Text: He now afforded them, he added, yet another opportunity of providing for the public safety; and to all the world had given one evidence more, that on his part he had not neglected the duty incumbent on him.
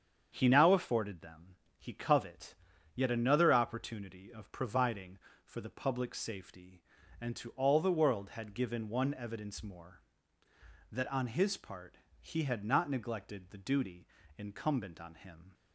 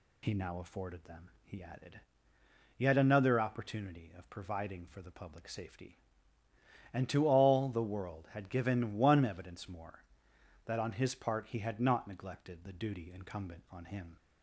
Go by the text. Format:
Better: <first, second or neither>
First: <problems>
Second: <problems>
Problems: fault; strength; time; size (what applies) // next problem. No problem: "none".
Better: second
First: starts louder than the rest; strong; until 1.3 s; 7.5 dB // says "covet" for "added"; at 1.9 s // pauses between "part" and "he"; slight; at 11.9 s; 0.22 s long // pauses between "duty" and "incumbent"; slight; at 14.0 s; 0.28 s long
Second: none